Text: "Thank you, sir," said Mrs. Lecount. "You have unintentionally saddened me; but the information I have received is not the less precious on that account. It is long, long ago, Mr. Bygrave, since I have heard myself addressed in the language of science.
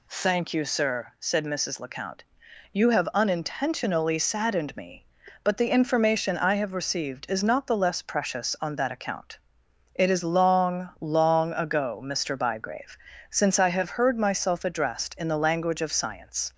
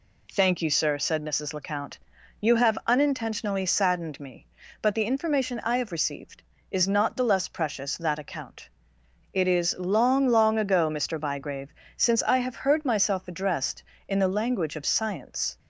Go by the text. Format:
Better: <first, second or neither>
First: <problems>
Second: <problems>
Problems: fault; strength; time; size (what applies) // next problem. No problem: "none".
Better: first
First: none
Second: skips "on"; at 7.9 s